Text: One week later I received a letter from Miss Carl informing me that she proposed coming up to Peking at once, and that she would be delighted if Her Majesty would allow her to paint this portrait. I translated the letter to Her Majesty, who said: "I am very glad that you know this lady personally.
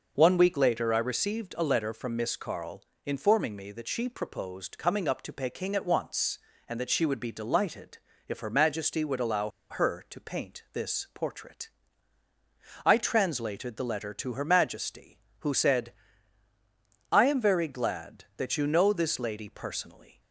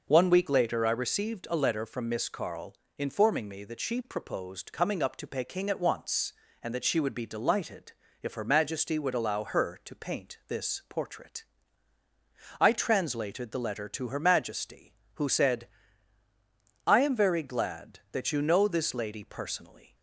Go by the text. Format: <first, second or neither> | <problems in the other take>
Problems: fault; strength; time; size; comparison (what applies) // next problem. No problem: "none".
second | pauses between "Carl" and "informing"; slight; at 2.8 s; 0.22 s long; slight in the second // pauses between "delighted" and "if"; slight; at 7.9 s; 0.28 s long; slight in the second // pauses between "allow" and "her"; slight; at 9.5 s; 0.19 s long